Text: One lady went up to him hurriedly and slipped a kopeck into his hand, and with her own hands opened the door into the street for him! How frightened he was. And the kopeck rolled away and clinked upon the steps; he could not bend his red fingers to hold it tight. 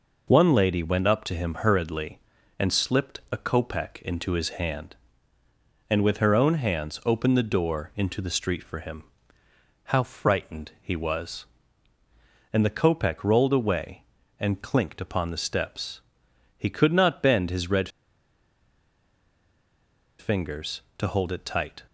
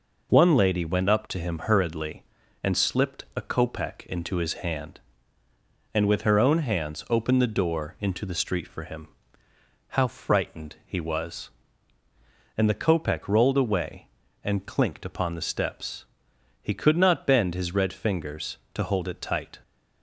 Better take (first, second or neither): second